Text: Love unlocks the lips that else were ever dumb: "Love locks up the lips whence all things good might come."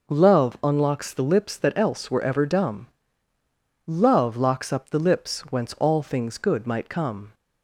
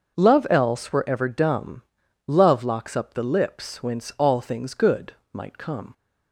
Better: first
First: none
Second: starts louder than the rest; noticeable; until 1.1 s; 6 dB // skips "unlocks the lips that"; at 0.4 s // pauses between "good" and "might"; slight; at 5.1 s; 0.22 s long

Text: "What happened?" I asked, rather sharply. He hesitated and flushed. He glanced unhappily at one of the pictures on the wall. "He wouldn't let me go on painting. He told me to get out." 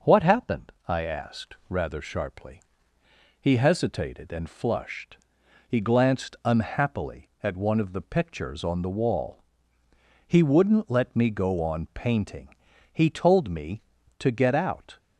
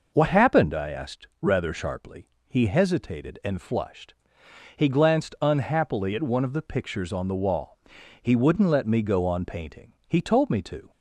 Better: first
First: none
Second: stops before "get out"; at 10.9 s

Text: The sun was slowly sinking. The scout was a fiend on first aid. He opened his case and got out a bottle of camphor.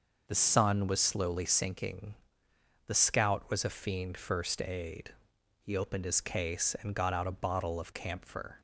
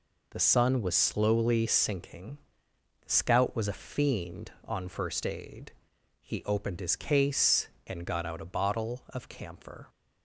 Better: second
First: skips "on"; at 4.1 s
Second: none

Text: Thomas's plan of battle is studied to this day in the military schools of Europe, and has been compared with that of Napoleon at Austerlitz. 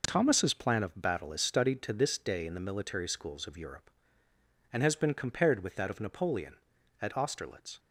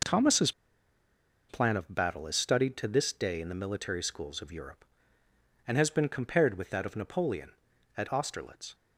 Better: first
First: none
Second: pauses between "Thomas's" and "plan"; at 0.5 s; 0.98 s long

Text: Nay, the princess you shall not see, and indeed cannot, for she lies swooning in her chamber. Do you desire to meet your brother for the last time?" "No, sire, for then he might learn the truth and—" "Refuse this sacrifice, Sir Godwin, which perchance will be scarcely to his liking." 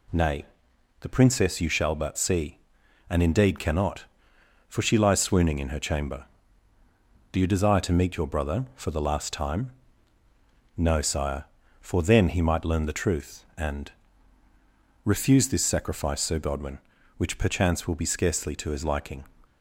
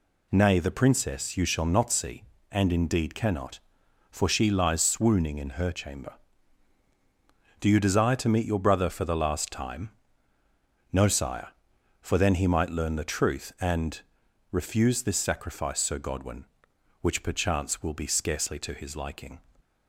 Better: second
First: says "but" for "not"; at 1.9 s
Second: none

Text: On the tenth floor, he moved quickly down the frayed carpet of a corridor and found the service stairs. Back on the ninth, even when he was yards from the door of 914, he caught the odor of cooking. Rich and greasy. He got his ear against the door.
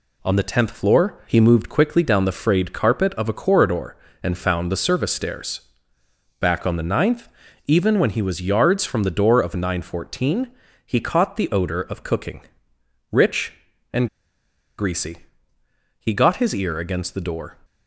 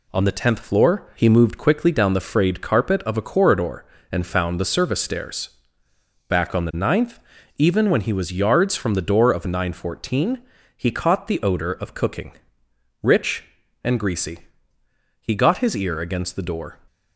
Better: second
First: pauses between "and" and "greasy"; noticeable; at 14.0 s; 0.70 s long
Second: none

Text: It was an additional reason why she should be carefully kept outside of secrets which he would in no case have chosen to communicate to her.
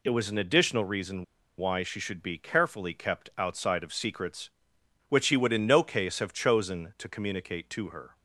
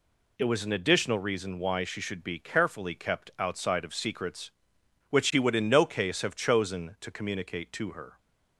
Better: second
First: pauses between "reason" and "why"; slight; at 1.2 s; 0.34 s long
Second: none

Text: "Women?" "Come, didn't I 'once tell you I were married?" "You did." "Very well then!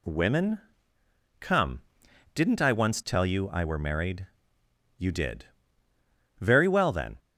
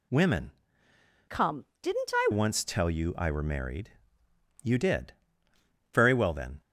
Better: first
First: none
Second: changes voice from "Come" to "I"; from 1.2 to 2.2 s; 1.0 s long

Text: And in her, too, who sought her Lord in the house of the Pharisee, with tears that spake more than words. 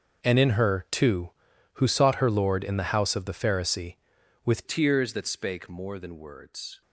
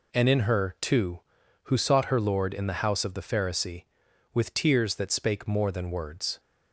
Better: second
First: starts louder than the rest; noticeable; until 1.2 s; 6 dB // changes voice at "tears"; from 4.6 s on; 2.2 s long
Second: none

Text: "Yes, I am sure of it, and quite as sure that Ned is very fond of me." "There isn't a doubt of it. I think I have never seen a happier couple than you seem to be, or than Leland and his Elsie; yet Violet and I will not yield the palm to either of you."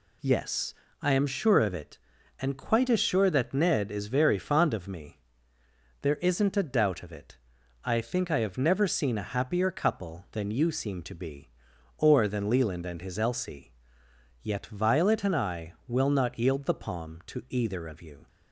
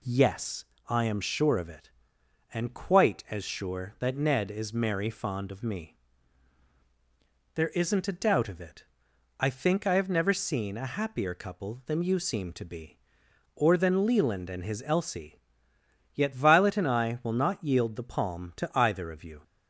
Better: first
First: none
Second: says "merry" for "very"; at 4.7 s

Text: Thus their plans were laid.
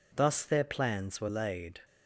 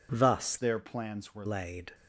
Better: first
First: none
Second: changes voice from "their" to "were"; from 0.5 to 1.4 s; 0.9 s long

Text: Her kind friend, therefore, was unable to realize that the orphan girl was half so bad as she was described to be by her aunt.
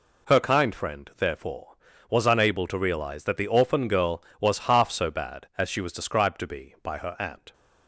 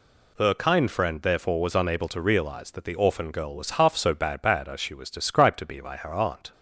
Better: first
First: none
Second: says "bad" twice; at 4.4 s

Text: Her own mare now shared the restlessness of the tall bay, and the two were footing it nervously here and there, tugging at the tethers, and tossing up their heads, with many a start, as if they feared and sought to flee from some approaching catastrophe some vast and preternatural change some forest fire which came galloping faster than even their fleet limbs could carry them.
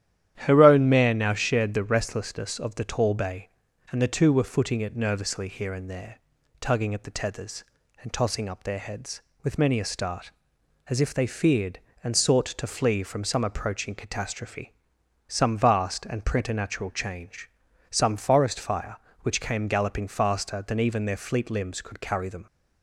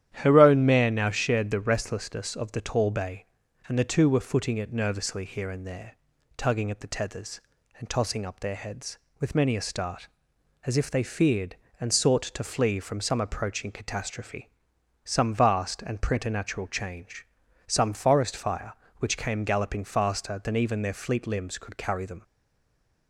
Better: first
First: starts louder than the rest; strong; until 1.3 s; 11 dB // pauses between "catastrophe" and "some"; noticeable; at 14.7 s; 0.56 s long // pauses between "change" and "some"; at 17.5 s; 0.40 s long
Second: starts louder than the rest; strong; until 1.1 s; 11 dB // pauses between "catastrophe" and "some"; noticeable; at 14.4 s; 0.56 s long // pauses between "change" and "some"; at 17.2 s; 0.40 s long // stays silent after the last word; slight; from 22.2 s on; 0.8 s long

